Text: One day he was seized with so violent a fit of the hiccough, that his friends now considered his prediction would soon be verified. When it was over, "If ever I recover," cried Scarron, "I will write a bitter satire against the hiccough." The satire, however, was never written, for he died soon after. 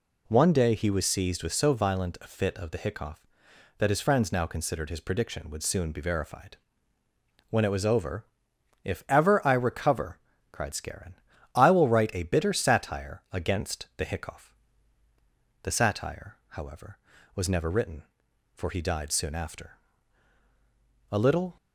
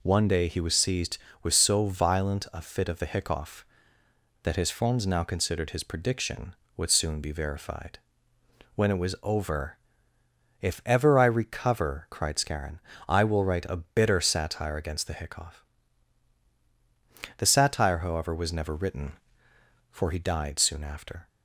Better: second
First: goes on to say "A little"; slight; from 21.1 s on; 0.44 s long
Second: none

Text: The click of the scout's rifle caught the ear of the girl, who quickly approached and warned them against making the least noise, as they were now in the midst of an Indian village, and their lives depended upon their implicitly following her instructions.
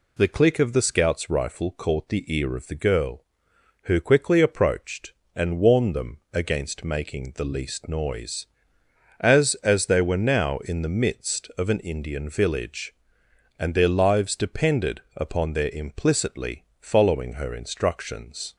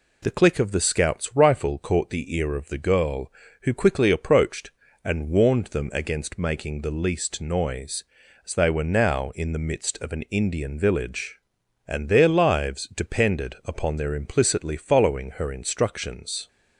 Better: second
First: pauses between "them" and "against"; slight; at 6.1 s; 0.16 s long // says "as" twice; at 9.6 s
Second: none

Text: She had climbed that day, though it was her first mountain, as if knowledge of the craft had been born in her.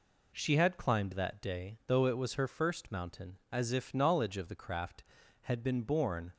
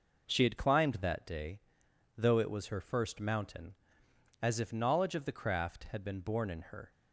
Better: second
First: stops before "in her"; at 6.3 s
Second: none

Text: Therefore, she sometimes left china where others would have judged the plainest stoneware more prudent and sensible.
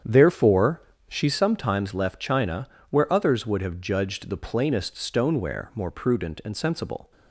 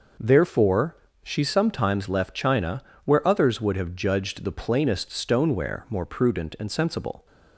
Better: second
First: starts louder than the rest; strong; until 1.5 s; 8.5 dB // pauses between "china" and "where"; slight; at 2.6 s; 0.22 s long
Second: pauses between "china" and "where"; slight; at 2.8 s; 0.22 s long

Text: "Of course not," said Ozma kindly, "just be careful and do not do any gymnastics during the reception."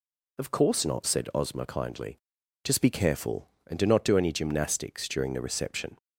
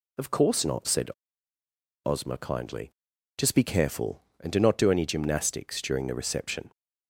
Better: first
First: none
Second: pauses between "said" and "Ozma"; noticeable; at 1.0 s; 0.98 s long

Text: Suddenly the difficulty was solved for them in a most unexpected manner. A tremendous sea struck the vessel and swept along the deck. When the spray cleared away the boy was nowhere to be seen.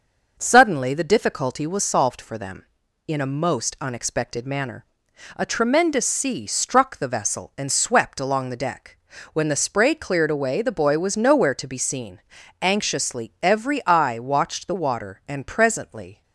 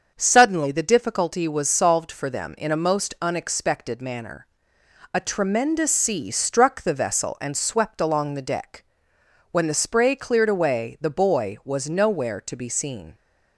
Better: second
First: starts louder than the rest; noticeable; until 1.3 s; 6 dB // goes on to say "Anxiously every eye watched the water and presently"; strong; from 12.6 s on; 3.6 s long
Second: starts louder than the rest; until 1.1 s; 6.5 dB

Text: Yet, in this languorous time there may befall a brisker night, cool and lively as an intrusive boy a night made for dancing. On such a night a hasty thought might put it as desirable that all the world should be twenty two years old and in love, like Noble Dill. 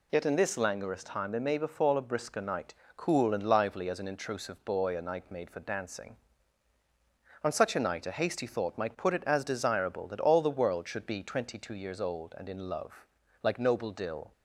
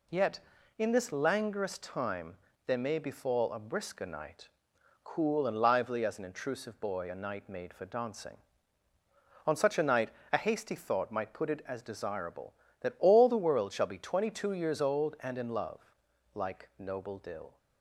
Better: first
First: none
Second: pauses between "time" and "there"; slight; at 2.3 s; 0.32 s long // pauses between "night" and "a"; slight; at 10.1 s; 0.20 s long // says "shall" for "should"; at 13.7 s

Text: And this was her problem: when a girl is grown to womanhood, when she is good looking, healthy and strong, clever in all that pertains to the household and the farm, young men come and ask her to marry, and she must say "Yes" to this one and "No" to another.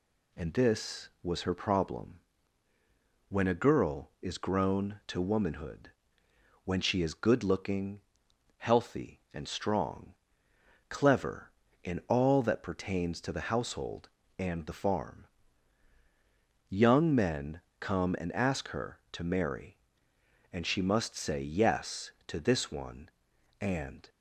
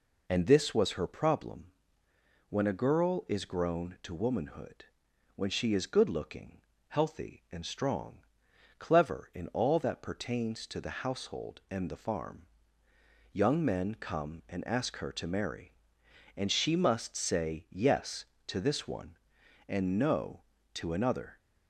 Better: second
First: pauses between "men" and "come"; slight; at 17.6 s; 0.18 s long // stops before "No to another"; at 24.0 s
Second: none

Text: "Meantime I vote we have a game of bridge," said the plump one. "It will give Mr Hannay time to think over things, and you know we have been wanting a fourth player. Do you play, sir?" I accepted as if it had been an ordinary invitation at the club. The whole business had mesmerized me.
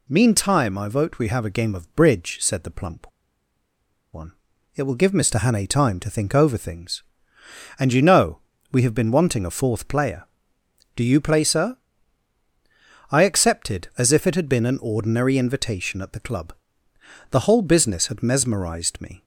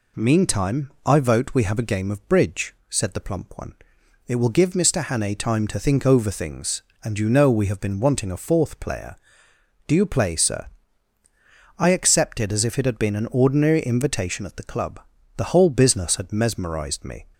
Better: second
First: pauses between "plump" and "one"; at 3.1 s; 1.0 s long // pauses between "know" and "we"; slight; at 8.3 s; 0.34 s long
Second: none

